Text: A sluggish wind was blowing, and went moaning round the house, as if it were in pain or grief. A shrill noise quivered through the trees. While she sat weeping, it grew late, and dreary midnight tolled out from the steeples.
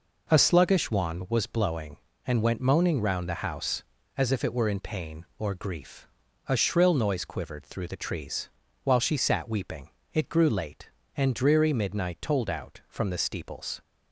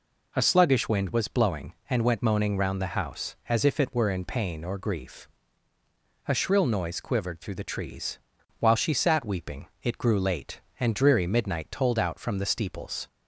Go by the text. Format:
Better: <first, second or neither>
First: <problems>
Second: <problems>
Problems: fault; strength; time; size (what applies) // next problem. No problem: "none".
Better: second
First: says "wand" for "wind"; at 0.9 s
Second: none